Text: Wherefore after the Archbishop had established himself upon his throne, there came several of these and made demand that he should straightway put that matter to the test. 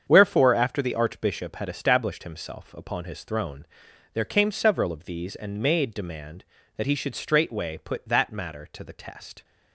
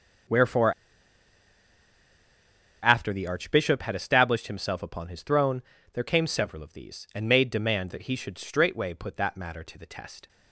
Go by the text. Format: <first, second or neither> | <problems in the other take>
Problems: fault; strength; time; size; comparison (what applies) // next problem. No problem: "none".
first | starts louder than the rest; until 3.3 s; 6 dB; strong in the first // pauses between "Wherefore" and "after"; strong; at 0.7 s; 2.0 s long